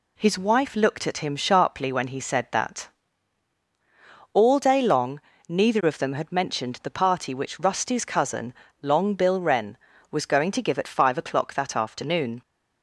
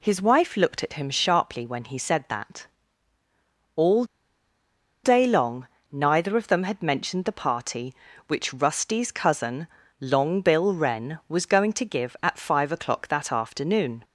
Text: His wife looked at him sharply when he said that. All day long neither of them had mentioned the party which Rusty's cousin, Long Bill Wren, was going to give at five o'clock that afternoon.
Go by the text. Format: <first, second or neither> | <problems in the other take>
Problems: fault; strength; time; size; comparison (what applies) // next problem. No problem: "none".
first | pauses between "All" and "day"; at 4.0 s; 1.0 s long // pauses between "long" and "neither"; slight; at 5.6 s; 0.26 s long; slight in the first